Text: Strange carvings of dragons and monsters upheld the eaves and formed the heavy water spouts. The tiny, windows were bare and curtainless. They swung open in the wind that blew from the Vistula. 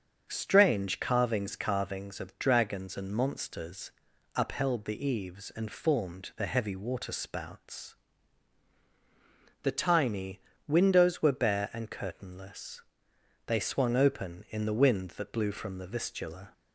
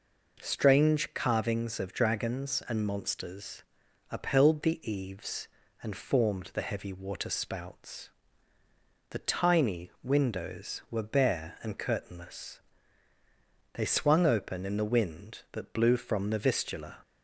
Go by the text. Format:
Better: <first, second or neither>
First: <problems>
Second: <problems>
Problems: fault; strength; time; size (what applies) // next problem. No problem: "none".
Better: second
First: starts louder than the rest; until 1.3 s; 7 dB // says "carvings" twice; at 1.5 s // pauses between "monsters" and "upheld"; at 3.9 s; 0.44 s long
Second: pauses between "monsters" and "upheld"; noticeable; at 3.6 s; 0.46 s long